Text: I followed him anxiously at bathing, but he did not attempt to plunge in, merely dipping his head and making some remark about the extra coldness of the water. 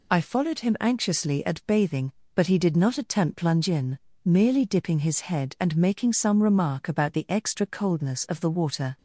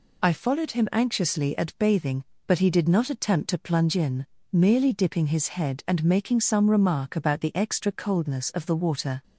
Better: second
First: skips "to"; at 3.3 s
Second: none

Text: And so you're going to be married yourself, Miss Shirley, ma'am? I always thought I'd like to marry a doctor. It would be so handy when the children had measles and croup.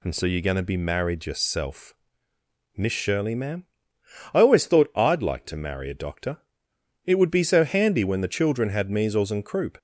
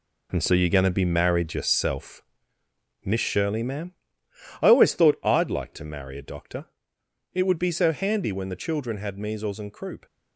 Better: first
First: none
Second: gets quieter; strong; throughout; 9 dB

